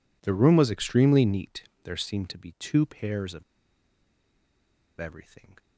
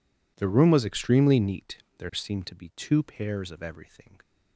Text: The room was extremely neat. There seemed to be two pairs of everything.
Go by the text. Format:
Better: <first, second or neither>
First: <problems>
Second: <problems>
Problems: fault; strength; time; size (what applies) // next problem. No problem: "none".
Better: second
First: pauses between "of" and "everything"; strong; at 3.4 s; 1.5 s long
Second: none